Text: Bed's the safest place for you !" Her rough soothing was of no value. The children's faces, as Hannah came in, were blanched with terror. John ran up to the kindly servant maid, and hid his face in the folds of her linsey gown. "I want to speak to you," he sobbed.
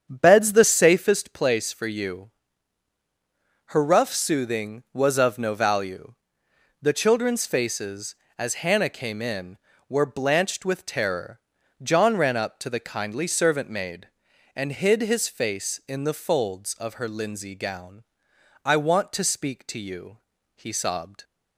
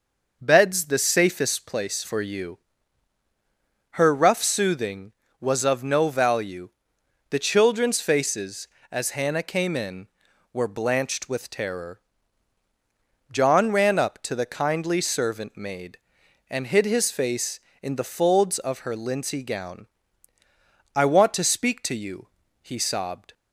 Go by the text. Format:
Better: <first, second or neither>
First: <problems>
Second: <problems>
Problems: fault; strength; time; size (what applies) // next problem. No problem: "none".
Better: second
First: starts louder than the rest; strong; until 1.2 s; 7.5 dB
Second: none